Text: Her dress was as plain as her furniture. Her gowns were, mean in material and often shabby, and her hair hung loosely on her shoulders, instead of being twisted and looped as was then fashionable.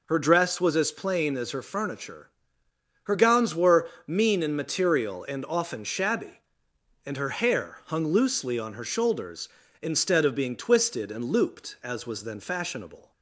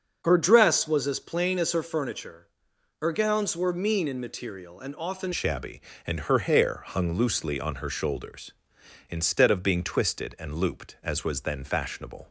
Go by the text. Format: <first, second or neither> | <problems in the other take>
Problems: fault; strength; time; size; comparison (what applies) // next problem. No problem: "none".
first | starts louder than the rest; until 1.2 s; 6.5 dB // changes voice at "shabby"; from 5.3 s on; 6.9 s long